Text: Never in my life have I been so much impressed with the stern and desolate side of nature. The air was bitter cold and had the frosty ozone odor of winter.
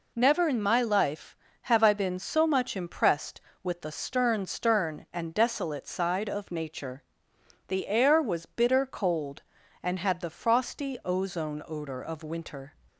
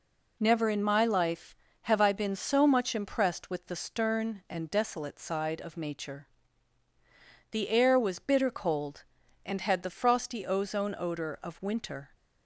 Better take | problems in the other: second | says "stern" twice; at 4.4 s

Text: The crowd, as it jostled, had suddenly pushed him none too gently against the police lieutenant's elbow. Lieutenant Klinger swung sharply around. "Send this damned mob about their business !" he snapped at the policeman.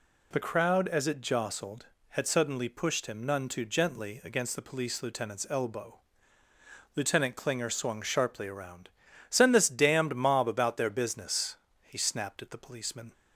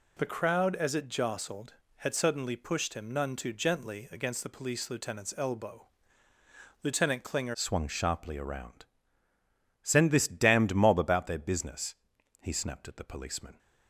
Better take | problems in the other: first | changes voice at "swung"; from 7.5 s on; 6.0 s long

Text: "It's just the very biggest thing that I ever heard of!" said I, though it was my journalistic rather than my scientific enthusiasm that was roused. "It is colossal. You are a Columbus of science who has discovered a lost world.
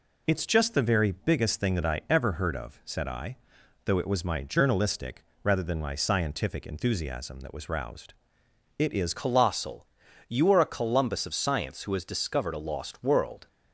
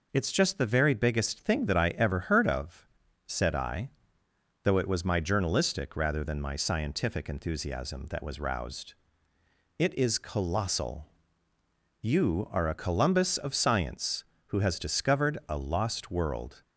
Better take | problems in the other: second | pauses between "journalistic" and "rather"; slight; at 5.2 s; 0.18 s long // changes voice at "colossal"; from 9.1 s on; 4.3 s long

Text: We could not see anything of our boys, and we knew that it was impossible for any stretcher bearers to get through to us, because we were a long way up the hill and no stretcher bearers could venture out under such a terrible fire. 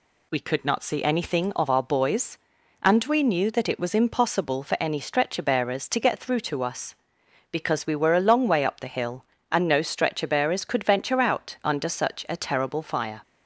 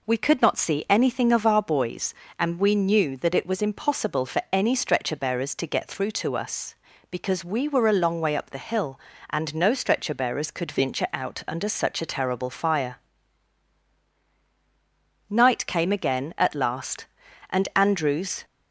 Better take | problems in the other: first | goes on to say "Night came again at last and Andrews"; strong; from 15.2 s on; 3.1 s long

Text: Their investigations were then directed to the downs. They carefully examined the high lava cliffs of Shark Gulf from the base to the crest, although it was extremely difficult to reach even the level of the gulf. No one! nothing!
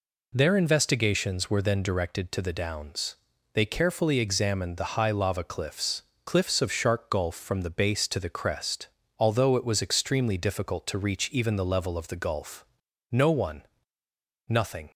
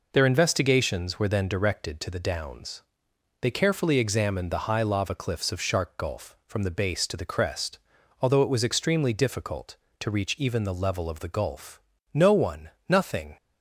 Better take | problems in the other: second | says "cliffs" twice; at 6.2 s

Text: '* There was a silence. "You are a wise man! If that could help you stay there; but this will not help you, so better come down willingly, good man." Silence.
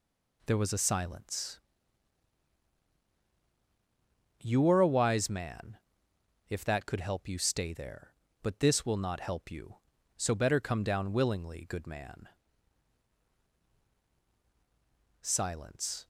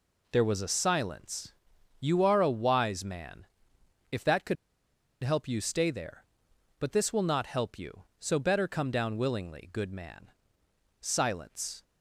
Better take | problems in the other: first | pauses between "could" and "help"; noticeable; at 4.5 s; 0.68 s long

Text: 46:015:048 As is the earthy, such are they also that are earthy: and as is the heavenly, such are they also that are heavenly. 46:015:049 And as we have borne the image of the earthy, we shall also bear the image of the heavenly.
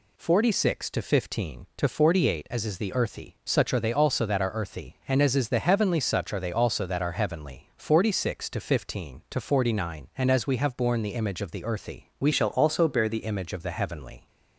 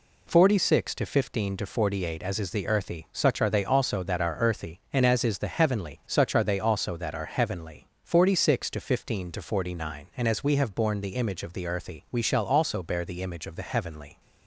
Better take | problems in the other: second | changes voice from "shall" to "the"; from 12.3 to 13.2 s; 0.9 s long

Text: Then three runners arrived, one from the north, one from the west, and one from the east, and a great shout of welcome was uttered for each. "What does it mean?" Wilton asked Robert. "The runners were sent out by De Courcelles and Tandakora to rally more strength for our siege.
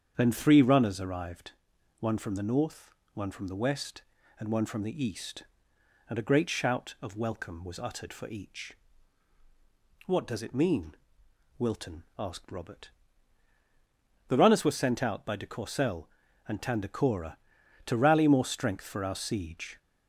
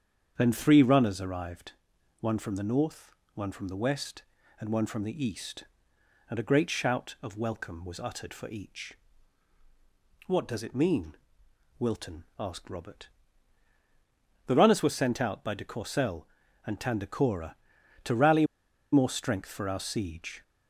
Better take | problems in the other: first | starts louder than the rest; strong; until 1.3 s; 7.5 dB; strong in the first // pauses between "rally" and "more"; noticeable; at 18.4 s; 0.48 s long

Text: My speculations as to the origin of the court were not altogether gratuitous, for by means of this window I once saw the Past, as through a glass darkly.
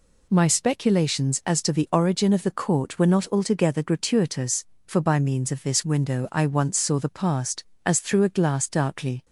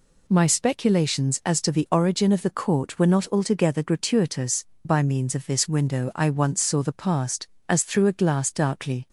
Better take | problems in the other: first | skips "for"; at 4.7 s

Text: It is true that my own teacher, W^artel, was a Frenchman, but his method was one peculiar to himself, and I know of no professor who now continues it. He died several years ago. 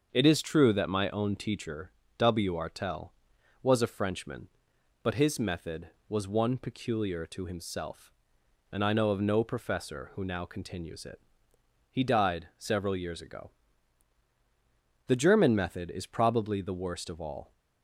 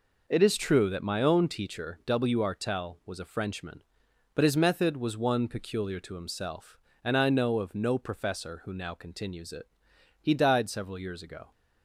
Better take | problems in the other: second | starts louder than the rest; until 1.1 s; 6.5 dB // goes on to say "The German method is probably the worst of all"; strong; from 15.0 s on; 2.4 s long

